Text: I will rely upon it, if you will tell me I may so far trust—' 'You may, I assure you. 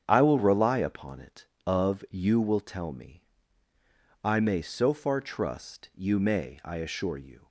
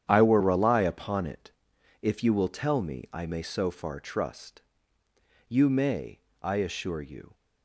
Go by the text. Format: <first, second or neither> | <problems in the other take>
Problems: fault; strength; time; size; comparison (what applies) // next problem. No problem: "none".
second | starts louder than the rest; strong; until 1.0 s; 8 dB; strong in the second // says "of" for "if"; at 1.6 s // pauses between "me" and "I"; at 3.2 s; 1.0 s long